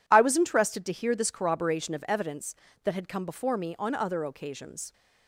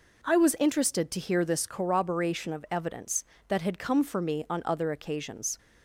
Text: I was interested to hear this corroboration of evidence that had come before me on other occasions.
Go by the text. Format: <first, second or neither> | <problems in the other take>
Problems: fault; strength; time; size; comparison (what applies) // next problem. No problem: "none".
first | says "for" for "before"; at 4.0 s